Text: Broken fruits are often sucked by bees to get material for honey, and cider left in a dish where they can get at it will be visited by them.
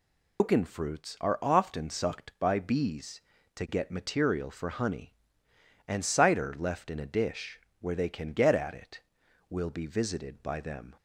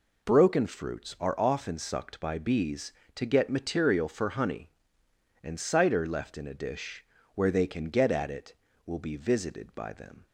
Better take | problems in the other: second | loses the start of "Broken"; at 0.3 s; 155 ms // pauses between "dish" and "where"; slight; at 7.6 s; 0.20 s long; slight in the second

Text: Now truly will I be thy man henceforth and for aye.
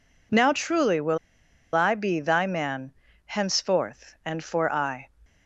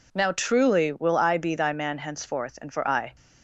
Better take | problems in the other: second | pauses between "will" and "I"; noticeable; at 1.1 s; 0.56 s long // pauses between "man" and "henceforth"; slight; at 2.9 s; 0.32 s long

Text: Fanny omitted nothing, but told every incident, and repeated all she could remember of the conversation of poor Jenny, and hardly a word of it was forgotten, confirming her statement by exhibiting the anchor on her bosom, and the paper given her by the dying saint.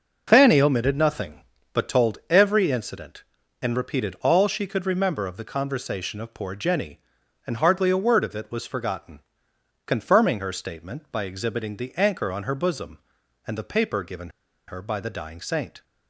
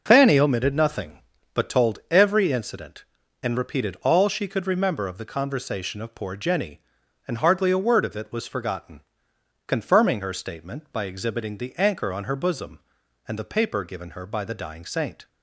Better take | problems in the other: second | pauses between "given" and "her"; at 14.2 s; 0.39 s long

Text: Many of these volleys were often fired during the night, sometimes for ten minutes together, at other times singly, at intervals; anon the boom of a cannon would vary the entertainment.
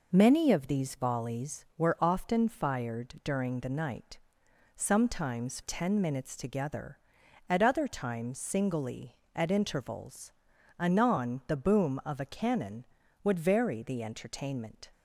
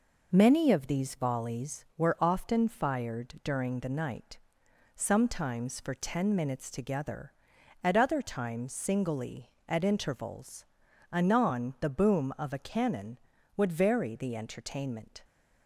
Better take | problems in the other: second | skips "for"; at 5.6 s

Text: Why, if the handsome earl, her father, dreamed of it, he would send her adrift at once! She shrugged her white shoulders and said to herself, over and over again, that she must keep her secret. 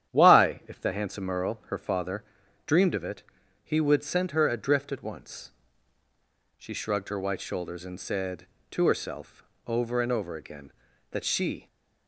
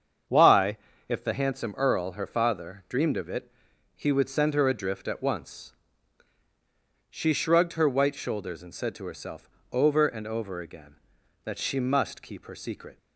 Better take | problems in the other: second | starts louder than the rest; strong; until 1.1 s; 10 dB; strong in the second // stops before "must keep her secret"; at 11.6 s

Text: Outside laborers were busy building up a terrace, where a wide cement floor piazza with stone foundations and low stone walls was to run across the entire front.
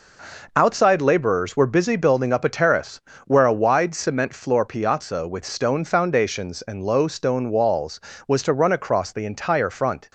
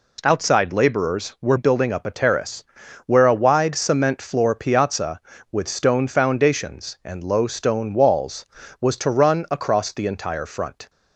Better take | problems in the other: first | skips "busy"; at 1.5 s

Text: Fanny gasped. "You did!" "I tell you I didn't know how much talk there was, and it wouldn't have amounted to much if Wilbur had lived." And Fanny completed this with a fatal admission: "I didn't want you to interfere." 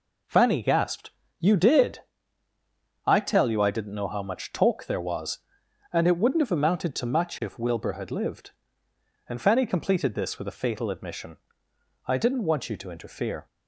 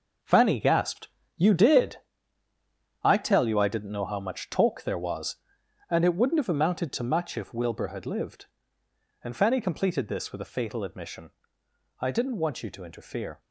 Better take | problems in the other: first | gets quieter; strong; throughout; 9 dB

